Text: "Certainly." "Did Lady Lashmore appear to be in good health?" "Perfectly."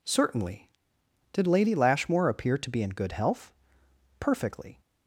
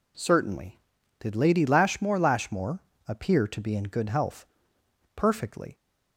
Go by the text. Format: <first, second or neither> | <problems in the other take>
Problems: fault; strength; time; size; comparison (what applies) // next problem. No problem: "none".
first | says "Lashmore" twice; at 2.1 s